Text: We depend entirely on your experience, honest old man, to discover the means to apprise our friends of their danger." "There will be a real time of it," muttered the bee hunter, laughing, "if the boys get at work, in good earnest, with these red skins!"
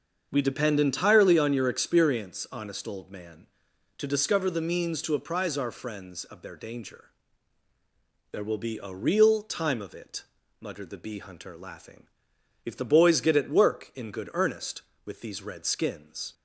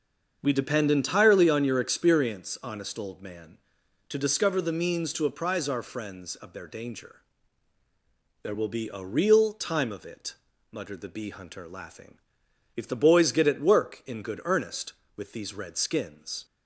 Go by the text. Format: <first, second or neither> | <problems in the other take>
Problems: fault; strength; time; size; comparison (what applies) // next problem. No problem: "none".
neither | starts louder than the rest; the same in both